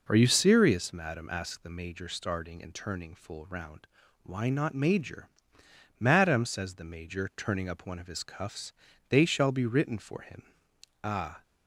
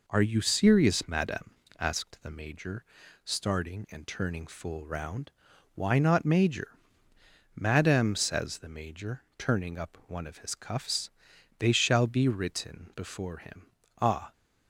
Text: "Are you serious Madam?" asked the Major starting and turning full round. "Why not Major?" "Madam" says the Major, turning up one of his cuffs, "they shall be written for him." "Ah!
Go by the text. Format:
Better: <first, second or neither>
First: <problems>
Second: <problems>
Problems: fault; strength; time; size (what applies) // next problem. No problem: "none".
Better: first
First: none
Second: pauses between "Major" and "starting"; at 2.8 s; 0.38 s long // says "before" for "for"; at 12.9 s